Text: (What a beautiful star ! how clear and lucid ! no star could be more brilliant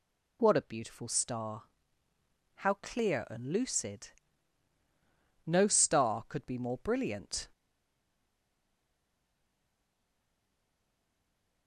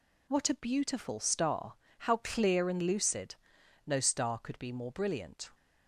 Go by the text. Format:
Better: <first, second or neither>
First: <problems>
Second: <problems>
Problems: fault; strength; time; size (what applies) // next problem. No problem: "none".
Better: second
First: stays silent after the last word; strong; from 7.5 s on; 4.1 s long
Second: none